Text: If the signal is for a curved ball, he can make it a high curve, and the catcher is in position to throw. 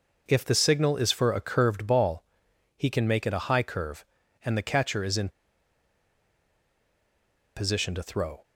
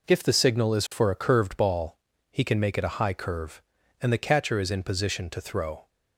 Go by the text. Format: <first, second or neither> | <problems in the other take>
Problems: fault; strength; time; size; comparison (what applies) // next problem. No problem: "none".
second | pauses between "in" and "position"; strong; at 5.2 s; 2.2 s long